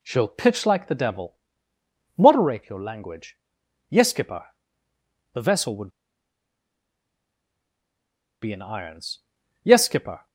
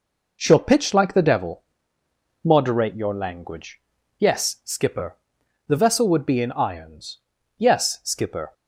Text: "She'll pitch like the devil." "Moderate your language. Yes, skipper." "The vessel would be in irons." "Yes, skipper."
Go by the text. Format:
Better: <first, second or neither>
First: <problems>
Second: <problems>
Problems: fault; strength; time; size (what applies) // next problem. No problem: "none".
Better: second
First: pauses between "would" and "be"; strong; at 5.8 s; 2.5 s long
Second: none